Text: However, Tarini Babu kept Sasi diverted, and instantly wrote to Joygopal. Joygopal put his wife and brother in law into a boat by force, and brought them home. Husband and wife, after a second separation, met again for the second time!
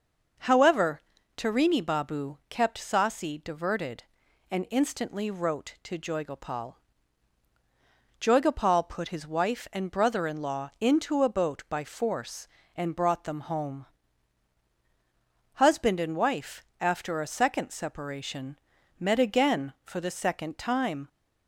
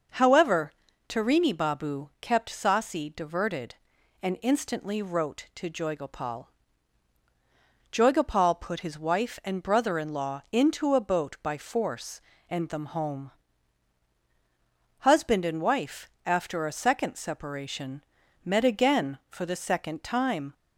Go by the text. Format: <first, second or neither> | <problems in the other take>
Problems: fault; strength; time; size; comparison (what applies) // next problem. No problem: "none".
first | skips "brought"; at 12.6 s